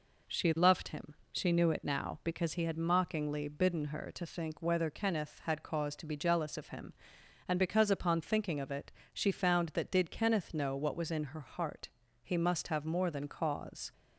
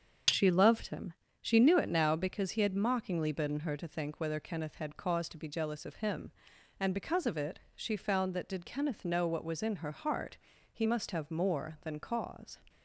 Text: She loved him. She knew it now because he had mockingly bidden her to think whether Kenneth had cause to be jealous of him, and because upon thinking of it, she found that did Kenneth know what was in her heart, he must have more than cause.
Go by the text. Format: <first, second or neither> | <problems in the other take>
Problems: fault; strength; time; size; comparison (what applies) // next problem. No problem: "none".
first | starts louder than the rest; until 1.5 s; 6.5 dB // skips "upon thinking"; at 7.2 s